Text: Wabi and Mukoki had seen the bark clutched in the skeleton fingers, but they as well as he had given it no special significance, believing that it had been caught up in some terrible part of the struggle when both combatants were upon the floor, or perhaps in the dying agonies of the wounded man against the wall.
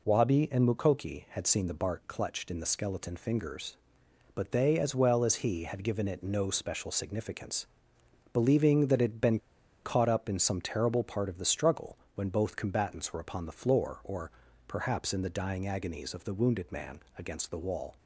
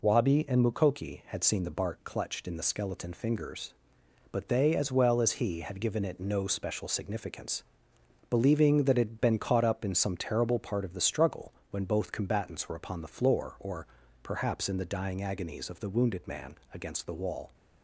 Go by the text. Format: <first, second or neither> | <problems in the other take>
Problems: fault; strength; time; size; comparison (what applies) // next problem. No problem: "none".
second | pauses between "been" and "caught"; noticeable; at 9.3 s; 0.46 s long // pauses between "struggle" and "when"; slight; at 11.9 s; 0.18 s long; slight in the second // pauses between "or" and "perhaps"; slight; at 14.3 s; 0.36 s long; slight in the second // pauses between "man" and "against"; slight; at 16.9 s; 0.18 s long; slight in the second